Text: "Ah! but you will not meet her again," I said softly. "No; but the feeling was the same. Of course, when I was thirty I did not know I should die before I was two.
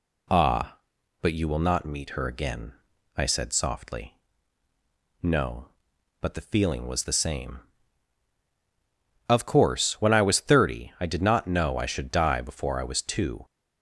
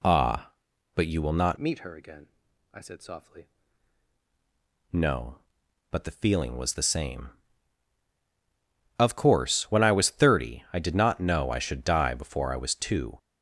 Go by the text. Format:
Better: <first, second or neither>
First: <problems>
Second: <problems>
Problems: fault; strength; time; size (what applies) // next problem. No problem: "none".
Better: first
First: none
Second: changes voice from "meet" to "softly"; from 1.5 to 3.4 s; 1.9 s long